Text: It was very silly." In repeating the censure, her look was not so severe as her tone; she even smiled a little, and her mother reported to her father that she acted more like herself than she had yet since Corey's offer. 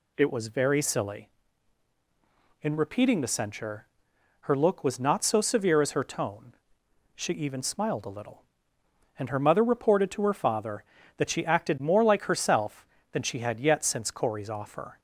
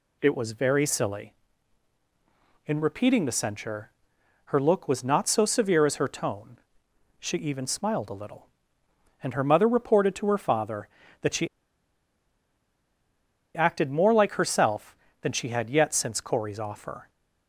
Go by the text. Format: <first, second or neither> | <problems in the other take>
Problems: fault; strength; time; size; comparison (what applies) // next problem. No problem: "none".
first | pauses between "she" and "acted"; strong; at 11.4 s; 2.0 s long